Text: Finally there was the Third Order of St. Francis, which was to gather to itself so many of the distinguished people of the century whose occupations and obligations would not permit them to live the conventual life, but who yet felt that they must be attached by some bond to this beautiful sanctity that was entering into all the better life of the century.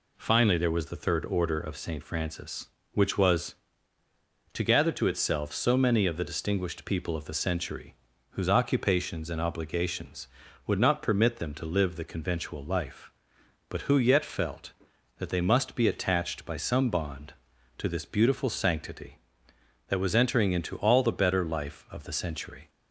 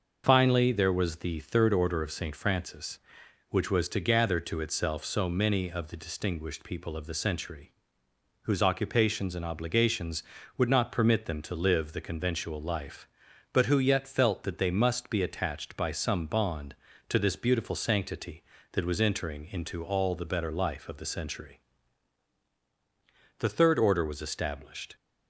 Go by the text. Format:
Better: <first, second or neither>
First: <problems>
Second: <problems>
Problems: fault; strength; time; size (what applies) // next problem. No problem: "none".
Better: first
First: pauses between "century" and "whose"; slight; at 7.9 s; 0.36 s long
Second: starts louder than the rest; noticeable; until 1.2 s; 6 dB // pauses between "century" and "whose"; noticeable; at 7.7 s; 0.70 s long // goes on to say "The Third Order was established"; from 23.3 s on; 1.5 s long